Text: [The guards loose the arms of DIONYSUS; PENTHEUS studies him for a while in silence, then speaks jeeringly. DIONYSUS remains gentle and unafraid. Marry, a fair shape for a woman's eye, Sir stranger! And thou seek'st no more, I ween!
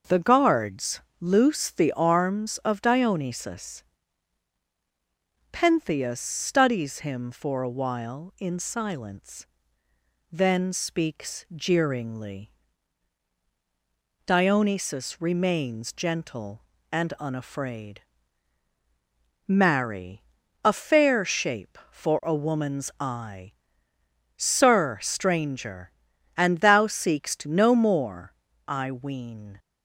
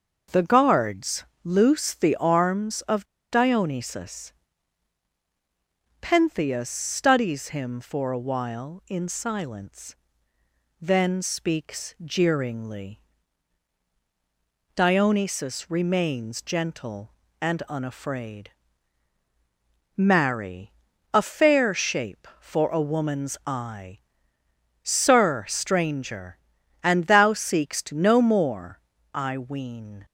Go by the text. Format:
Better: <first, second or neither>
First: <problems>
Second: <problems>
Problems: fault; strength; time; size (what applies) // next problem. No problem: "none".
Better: first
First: starts louder than the rest; noticeable; until 1.2 s; 6 dB // pauses between "guards" and "loose"; slight; at 0.9 s; 0.20 s long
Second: starts louder than the rest; noticeable; until 1.5 s; 6 dB // pauses between "guards" and "loose"; slight; at 1.2 s; 0.20 s long // pauses between "of" and "DIONYSUS"; slight; at 3.0 s; 0.28 s long